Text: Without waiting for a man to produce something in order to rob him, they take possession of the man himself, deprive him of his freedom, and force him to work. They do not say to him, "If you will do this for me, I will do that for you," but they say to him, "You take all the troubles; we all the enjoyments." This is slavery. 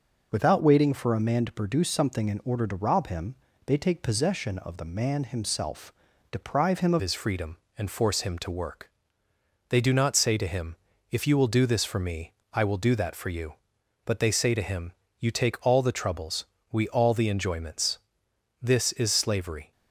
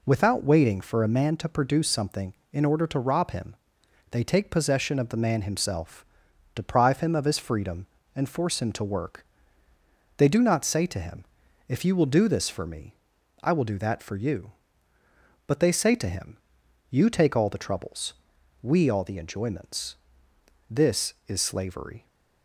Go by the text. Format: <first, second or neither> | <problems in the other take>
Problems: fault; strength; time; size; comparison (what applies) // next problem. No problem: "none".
second | changes voice at "his"; from 6.9 s on; 12.8 s long